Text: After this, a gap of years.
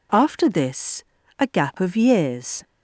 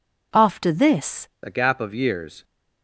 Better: first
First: none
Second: changes voice at "a"; from 1.4 s on; 1.0 s long

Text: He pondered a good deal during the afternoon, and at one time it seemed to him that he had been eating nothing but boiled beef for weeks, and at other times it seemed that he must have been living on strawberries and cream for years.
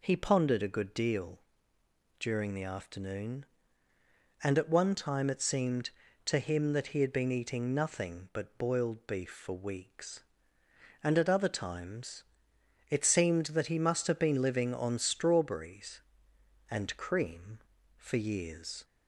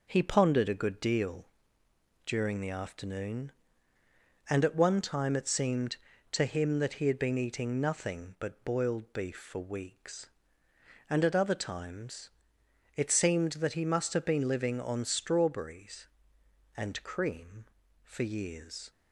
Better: first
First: pauses between "deal" and "during"; noticeable; at 1.4 s; 0.78 s long // pauses between "times" and "it"; noticeable; at 12.2 s; 0.66 s long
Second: gets quieter; noticeable; throughout; 5 dB // pauses between "deal" and "during"; noticeable; at 1.4 s; 0.78 s long // pauses between "times" and "it"; noticeable; at 12.3 s; 0.66 s long

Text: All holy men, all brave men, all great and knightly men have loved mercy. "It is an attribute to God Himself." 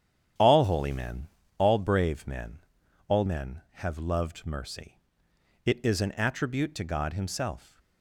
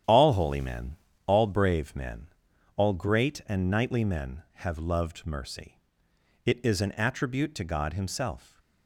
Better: second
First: starts louder than the rest; strong; until 1.6 s; 9.5 dB // skips "great and knightly"; at 3.2 s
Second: starts louder than the rest; strong; until 1.3 s; 9.5 dB

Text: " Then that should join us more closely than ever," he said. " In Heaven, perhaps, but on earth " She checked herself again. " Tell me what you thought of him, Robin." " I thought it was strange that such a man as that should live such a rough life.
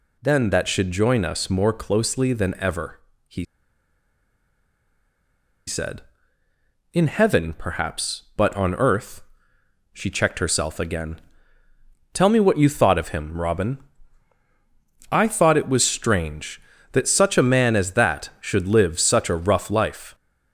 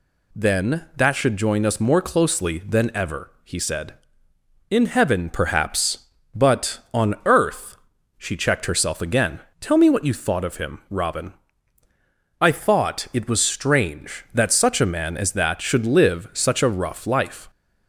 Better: second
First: pauses between "he" and "said"; strong; at 3.4 s; 2.2 s long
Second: none

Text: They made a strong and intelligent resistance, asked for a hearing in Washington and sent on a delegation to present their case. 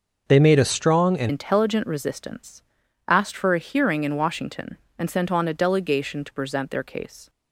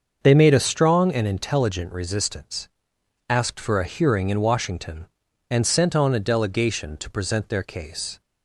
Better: second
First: starts louder than the rest; until 1.2 s; 6 dB // changes voice at "intelligent"; from 1.2 s on; 6.0 s long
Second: starts louder than the rest; until 1.2 s; 6.5 dB

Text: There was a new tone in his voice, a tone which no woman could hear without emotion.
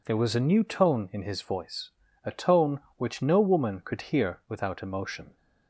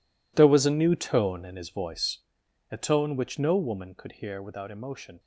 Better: first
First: none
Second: gets quieter; strong; throughout; 15.5 dB

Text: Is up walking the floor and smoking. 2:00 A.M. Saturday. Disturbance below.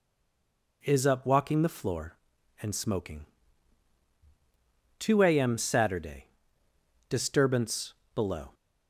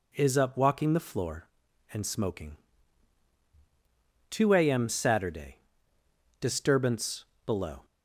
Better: second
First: stays silent before the first word; slight; until 0.8 s; 0.8 s long // pauses between "Disturbance" and "below"; slight; at 7.9 s; 0.22 s long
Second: pauses between "Disturbance" and "below"; slight; at 7.2 s; 0.22 s long

